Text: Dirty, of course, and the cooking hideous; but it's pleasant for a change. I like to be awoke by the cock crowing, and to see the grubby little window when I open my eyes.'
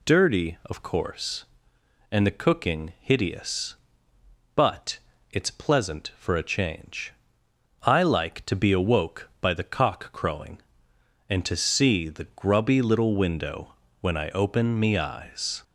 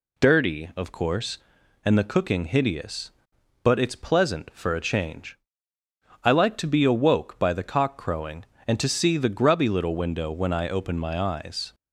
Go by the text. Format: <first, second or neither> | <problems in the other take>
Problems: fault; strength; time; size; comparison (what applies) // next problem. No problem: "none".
second | pauses between "but" and "it's"; slight; at 4.9 s; 0.32 s long // pauses between "window" and "when"; slight; at 13.7 s; 0.26 s long // says "me" for "my"; at 14.7 s